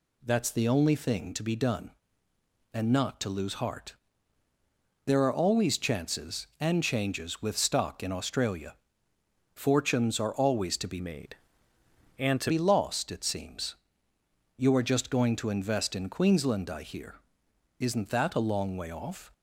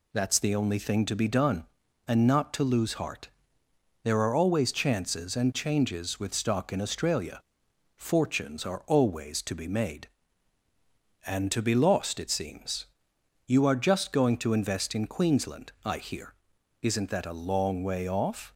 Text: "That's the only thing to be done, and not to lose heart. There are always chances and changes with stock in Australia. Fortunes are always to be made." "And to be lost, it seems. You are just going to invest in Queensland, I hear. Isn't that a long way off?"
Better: second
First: changes voice from "made" to "to"; from 10.9 to 12.5 s; 1.6 s long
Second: none

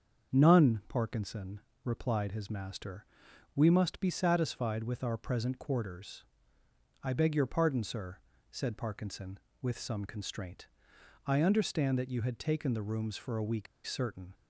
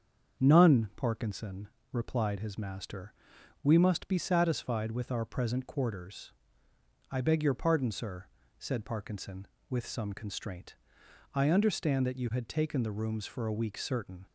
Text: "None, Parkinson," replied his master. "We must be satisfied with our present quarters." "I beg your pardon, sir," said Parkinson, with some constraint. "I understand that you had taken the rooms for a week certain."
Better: second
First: starts louder than the rest; until 1.4 s; 6.5 dB // pauses between "week" and "certain"; slight; at 13.6 s; 0.19 s long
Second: starts louder than the rest; until 1.4 s; 6.5 dB

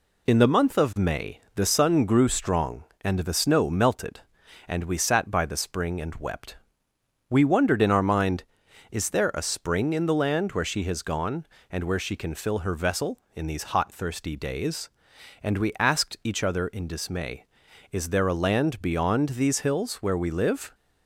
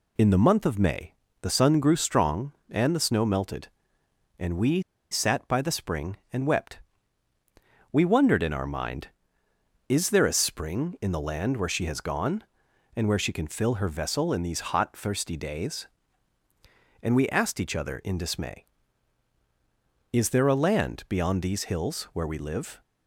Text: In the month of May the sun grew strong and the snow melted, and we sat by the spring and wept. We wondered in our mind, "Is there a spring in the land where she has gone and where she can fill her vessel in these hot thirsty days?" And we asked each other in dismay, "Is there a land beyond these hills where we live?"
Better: first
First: none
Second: pauses between "May" and "the"; slight; at 1.1 s; 0.30 s long // pauses between "we" and "sat"; slight; at 4.7 s; 0.31 s long

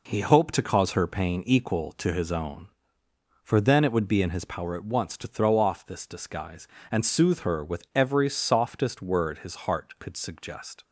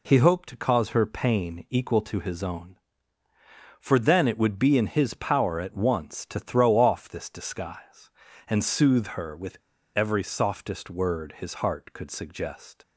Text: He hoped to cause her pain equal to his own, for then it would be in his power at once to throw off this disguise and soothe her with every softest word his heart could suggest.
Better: first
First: none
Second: pauses between "with" and "every"; at 9.5 s; 0.39 s long

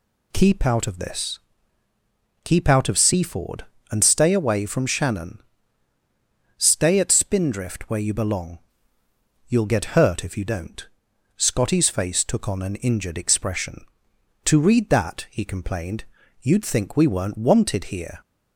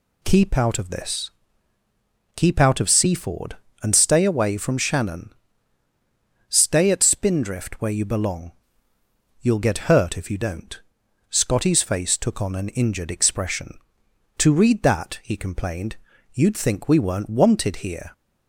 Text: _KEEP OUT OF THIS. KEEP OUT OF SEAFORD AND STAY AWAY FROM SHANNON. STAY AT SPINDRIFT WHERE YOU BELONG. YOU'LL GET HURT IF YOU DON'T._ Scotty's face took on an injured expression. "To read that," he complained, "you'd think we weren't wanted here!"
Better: neither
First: none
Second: none

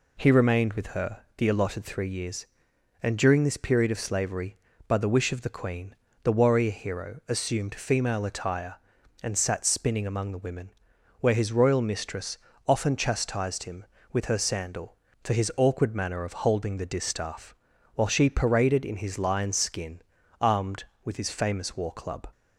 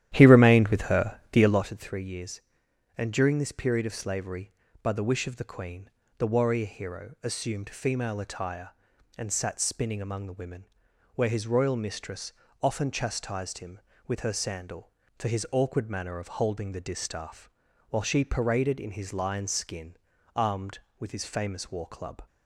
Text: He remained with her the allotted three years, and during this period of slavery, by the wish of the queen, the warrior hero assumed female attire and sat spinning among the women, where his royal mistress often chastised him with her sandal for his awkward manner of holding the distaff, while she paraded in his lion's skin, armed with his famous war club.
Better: first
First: pauses between "mistress" and "often"; slight; at 12.3 s; 0.30 s long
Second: starts louder than the rest; strong; until 1.7 s; 12 dB // pauses between "mistress" and "often"; slight; at 12.3 s; 0.30 s long

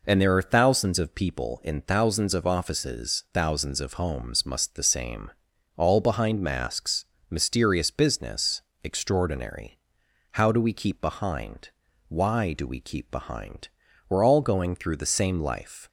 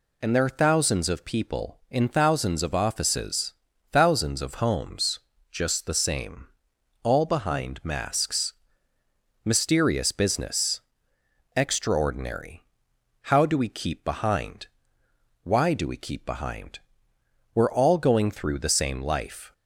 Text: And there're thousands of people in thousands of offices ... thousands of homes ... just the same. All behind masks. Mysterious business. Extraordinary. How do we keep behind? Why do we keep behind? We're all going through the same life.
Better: second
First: says "must" for "just"; at 4.4 s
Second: none

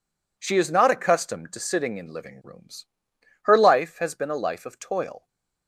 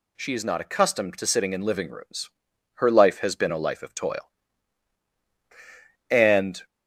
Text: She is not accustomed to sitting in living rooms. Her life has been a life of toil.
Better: first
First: none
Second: goes on to say "And"; from 6.0 s on; 0.56 s long

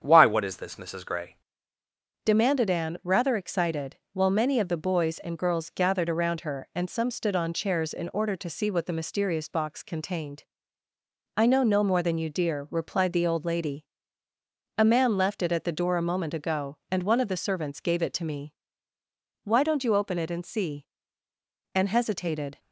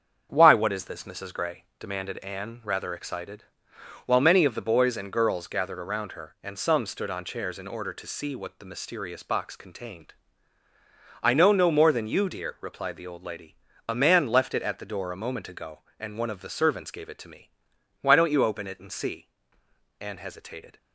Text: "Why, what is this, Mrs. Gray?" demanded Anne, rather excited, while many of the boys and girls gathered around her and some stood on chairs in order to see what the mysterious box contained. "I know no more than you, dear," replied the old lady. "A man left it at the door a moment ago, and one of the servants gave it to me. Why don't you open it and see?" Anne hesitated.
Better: second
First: starts louder than the rest; strong; until 1.0 s; 8 dB // changes voice at "demanded"; from 2.2 s on; 20.3 s long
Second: starts louder than the rest; strong; until 1.3 s; 7 dB

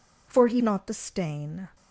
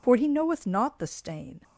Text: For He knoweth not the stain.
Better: second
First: skips "knoweth"; at 0.6 s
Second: none

